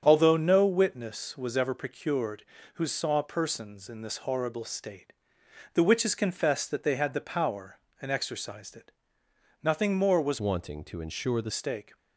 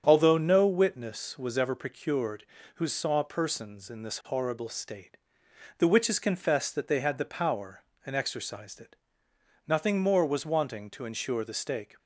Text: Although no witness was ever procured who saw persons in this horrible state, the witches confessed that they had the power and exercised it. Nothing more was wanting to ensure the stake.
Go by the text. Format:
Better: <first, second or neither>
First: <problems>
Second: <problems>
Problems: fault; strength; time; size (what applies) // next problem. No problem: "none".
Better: second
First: starts louder than the rest; strong; until 1.0 s; 7.5 dB // changes voice from "wanting" to "the"; from 10.3 to 11.5 s; 1.2 s long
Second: starts louder than the rest; strong; until 1.0 s; 7.5 dB